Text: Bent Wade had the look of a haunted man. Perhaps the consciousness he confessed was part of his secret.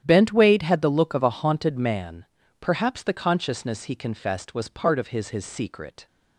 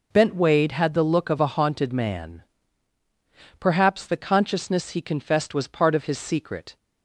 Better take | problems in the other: second | starts louder than the rest; strong; until 1.0 s; 10 dB // says "his" twice; at 5.2 s

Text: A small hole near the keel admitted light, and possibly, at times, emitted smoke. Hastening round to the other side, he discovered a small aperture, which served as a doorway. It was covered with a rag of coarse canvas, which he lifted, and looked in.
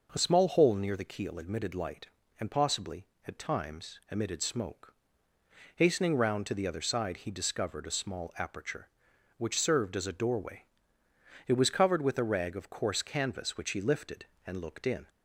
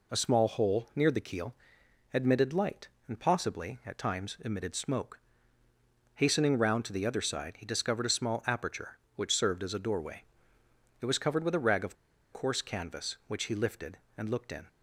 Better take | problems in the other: first | pauses between "keel" and "admitted"; noticeable; at 1.5 s; 0.58 s long // pauses between "of" and "coarse"; at 11.9 s; 0.38 s long

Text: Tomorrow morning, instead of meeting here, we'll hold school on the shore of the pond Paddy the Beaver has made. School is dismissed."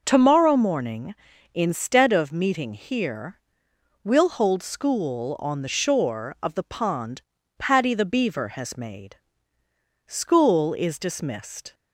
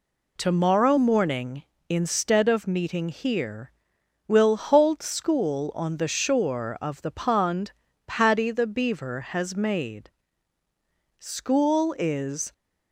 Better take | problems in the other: first | pauses between "pond" and "Paddy"; slight; at 7.7 s; 0.34 s long; also in the first // stops before "dismissed"; at 12.5 s

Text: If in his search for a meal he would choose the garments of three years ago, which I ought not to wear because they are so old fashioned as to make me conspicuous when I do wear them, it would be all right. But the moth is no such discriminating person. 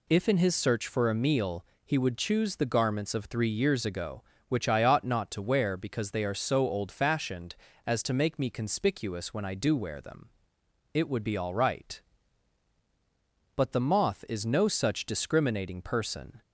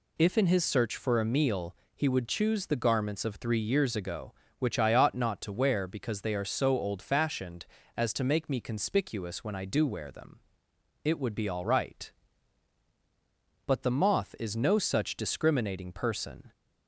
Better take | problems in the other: neither | pauses between "meal" and "he"; slight; the same in both

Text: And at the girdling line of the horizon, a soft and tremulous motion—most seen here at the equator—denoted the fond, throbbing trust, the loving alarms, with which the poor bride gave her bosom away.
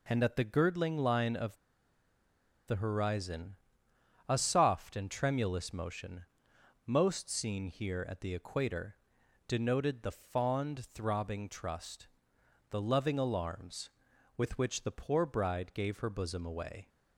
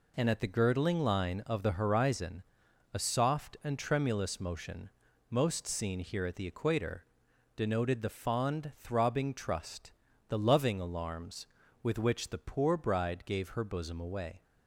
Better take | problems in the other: second | pauses between "of" and "the"; at 1.5 s; 1.1 s long

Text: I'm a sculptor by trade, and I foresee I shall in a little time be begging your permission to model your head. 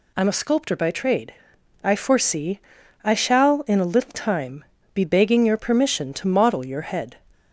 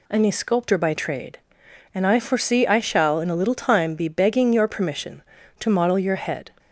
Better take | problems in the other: second | skips "and"; at 1.5 s // pauses between "foresee" and "I"; at 2.5 s; 0.44 s long // pauses between "time" and "be"; slight; at 4.6 s; 0.30 s long

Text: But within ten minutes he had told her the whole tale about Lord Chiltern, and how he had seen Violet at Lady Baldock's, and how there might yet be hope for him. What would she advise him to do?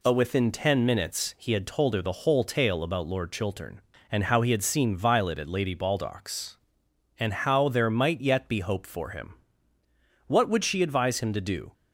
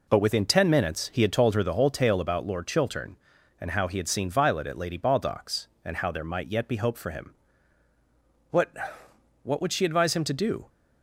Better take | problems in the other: first | says "What" twice; at 9.4 s

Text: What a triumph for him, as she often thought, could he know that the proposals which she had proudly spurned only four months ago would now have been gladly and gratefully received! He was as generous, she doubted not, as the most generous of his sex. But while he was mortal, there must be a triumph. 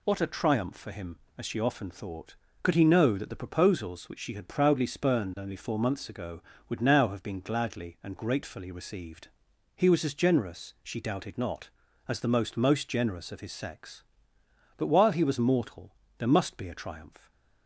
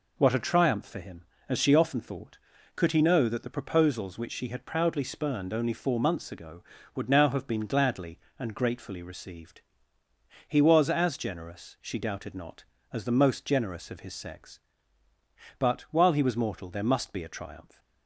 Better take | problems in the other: second | says "most" twice; at 12.5 s

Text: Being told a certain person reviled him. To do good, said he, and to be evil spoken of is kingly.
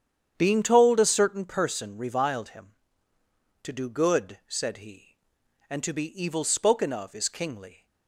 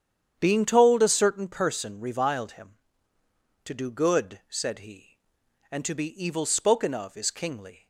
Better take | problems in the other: neither | starts louder than the rest; strong; the same in both

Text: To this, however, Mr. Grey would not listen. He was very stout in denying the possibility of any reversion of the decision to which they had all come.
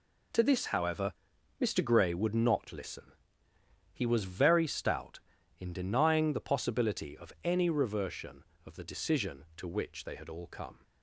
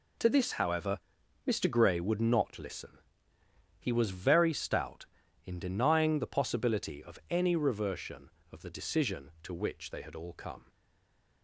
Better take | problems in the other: first | stays silent after the last word; slight; from 10.6 s on; 0.8 s long

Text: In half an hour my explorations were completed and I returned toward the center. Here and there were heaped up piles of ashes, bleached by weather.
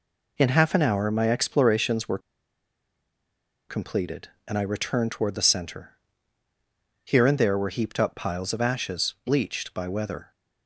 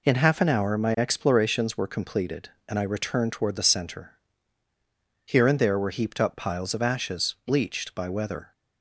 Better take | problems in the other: second | pauses between "were" and "completed"; strong; at 2.1 s; 1.5 s long

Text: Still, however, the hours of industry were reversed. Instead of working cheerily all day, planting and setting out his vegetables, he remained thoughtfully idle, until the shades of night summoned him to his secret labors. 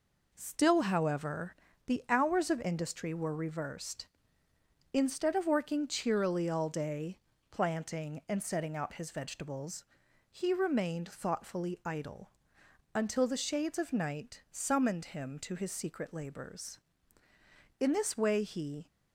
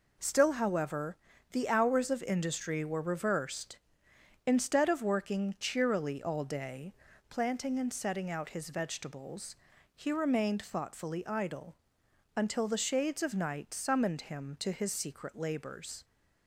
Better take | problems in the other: second | goes on to say "In this way he"; noticeable; from 17.7 s on; 1.0 s long

